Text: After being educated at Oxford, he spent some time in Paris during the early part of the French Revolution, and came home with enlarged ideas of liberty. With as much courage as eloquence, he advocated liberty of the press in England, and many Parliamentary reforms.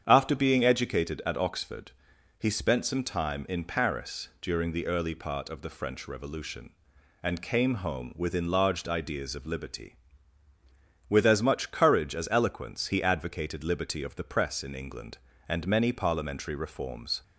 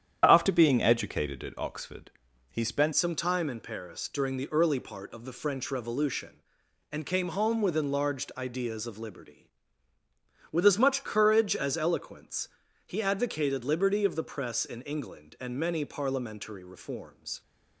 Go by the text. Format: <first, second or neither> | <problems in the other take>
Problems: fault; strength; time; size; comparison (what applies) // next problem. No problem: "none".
first | starts louder than the rest; strong; until 1.2 s; 9 dB; strong in the first // changes voice at "some"; from 2.9 s on; 14.5 s long